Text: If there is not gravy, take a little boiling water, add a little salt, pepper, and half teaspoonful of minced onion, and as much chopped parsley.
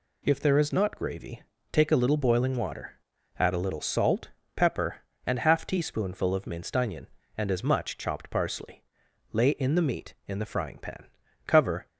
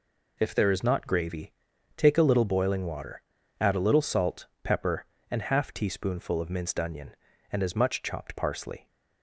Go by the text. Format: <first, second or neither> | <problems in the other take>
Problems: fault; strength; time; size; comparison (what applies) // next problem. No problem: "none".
second | goes on to say "Lay in the meat in the frying pan cover"; strong; from 9.3 s on; 2.5 s long